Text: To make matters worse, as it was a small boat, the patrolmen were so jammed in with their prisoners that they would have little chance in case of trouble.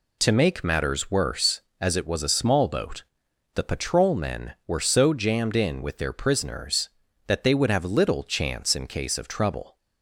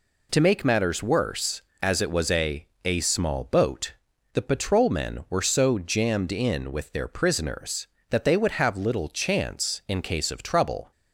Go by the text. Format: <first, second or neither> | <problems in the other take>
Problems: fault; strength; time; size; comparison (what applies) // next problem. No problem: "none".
first | says "a" twice; at 2.8 s